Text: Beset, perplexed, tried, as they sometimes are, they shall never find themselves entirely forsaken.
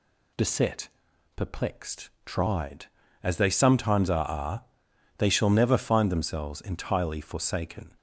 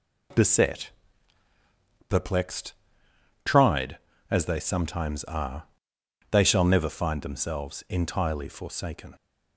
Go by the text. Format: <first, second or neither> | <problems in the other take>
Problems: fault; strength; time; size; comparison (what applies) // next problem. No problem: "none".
second | says "are" twice; at 4.2 s